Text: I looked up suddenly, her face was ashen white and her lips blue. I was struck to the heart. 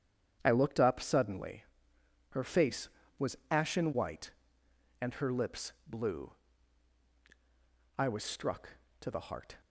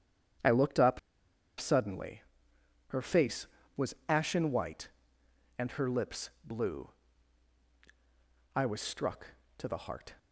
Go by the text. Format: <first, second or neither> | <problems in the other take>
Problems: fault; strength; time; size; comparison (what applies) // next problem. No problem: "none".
first | starts louder than the rest; strong; until 2.0 s; 9 dB; strong in the first // pauses between "up" and "suddenly"; noticeable; at 0.9 s; 0.61 s long